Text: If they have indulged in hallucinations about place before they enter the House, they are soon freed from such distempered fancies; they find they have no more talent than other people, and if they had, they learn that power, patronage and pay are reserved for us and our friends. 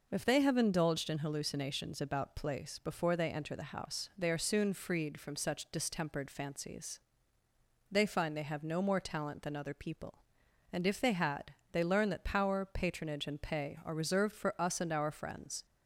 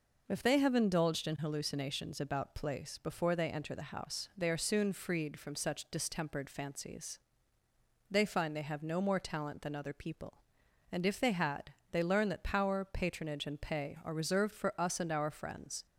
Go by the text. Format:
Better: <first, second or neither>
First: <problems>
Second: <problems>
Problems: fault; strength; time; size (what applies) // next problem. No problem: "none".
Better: neither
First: none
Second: none